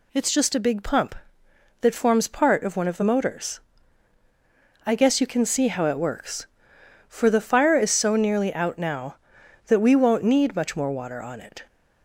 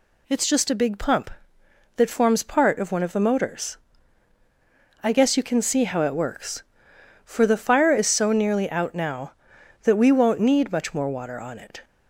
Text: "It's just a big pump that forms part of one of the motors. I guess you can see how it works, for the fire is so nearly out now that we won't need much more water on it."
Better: neither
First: none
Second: none

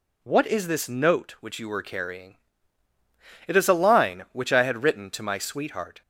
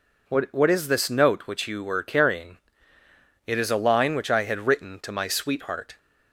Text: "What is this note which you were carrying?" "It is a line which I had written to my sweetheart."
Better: first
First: none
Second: says "What" twice; at 0.5 s

